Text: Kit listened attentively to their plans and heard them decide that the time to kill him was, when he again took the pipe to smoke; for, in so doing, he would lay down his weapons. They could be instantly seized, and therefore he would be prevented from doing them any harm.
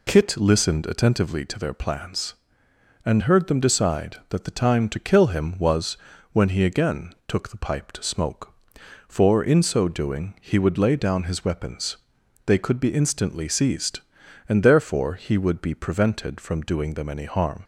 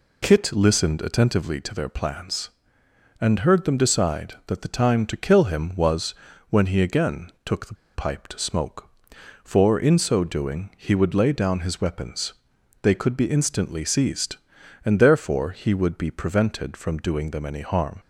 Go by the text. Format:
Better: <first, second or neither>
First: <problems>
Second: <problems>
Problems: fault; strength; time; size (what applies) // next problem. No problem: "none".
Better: first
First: none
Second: pauses between "the" and "pipe"; slight; at 7.7 s; 0.20 s long